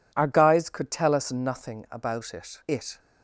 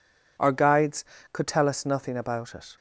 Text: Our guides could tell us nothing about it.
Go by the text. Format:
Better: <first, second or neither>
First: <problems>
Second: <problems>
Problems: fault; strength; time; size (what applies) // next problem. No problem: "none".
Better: second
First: says "it" twice; at 2.6 s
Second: none